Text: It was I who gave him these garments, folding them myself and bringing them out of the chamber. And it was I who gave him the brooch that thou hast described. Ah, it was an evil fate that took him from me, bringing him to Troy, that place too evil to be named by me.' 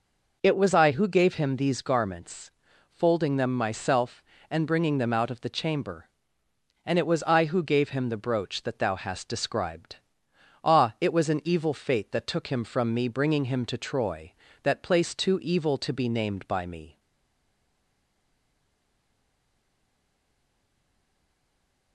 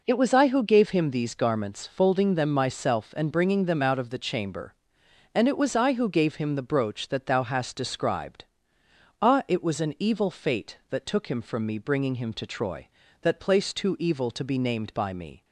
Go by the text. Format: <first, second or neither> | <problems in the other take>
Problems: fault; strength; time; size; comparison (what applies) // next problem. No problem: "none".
second | stays silent after the last word; strong; from 16.9 s on; 5.0 s long